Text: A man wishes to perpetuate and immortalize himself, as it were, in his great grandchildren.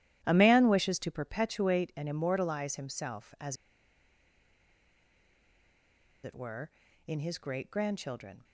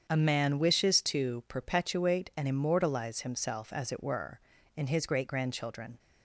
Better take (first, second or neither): second